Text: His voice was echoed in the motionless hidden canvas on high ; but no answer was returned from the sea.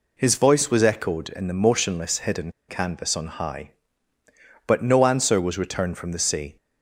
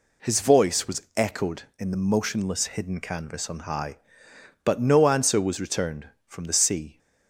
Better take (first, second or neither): second